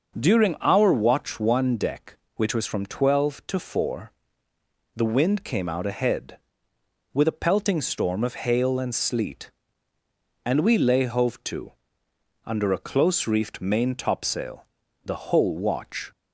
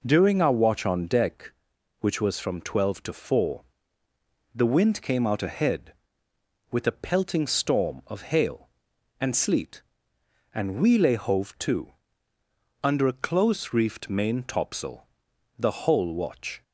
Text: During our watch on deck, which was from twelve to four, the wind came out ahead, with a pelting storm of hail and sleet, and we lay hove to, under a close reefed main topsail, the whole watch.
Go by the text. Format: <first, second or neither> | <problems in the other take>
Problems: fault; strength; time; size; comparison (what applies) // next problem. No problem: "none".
second | starts louder than the rest; noticeable; until 1.2 s; 6 dB // says "one" for "on"; at 1.3 s